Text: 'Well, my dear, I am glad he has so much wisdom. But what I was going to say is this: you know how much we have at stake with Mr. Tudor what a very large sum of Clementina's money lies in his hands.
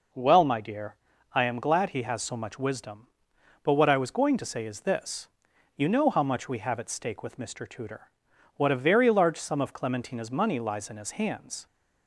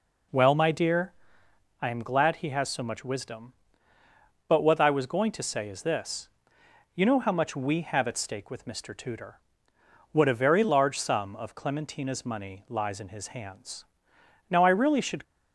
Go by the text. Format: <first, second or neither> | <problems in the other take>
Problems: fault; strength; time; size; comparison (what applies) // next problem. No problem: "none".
first | pauses between "Tudor" and "what"; noticeable; at 9.3 s; 0.74 s long; noticeable in the first // goes on to say "Now I really should"; noticeable; from 14.5 s on; 0.72 s long